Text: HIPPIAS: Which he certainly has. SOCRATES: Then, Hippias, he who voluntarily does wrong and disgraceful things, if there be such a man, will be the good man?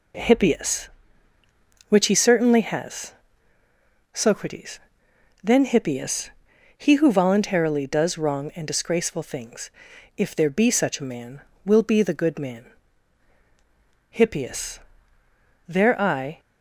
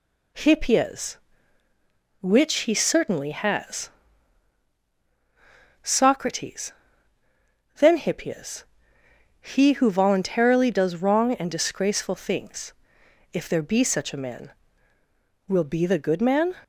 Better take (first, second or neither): second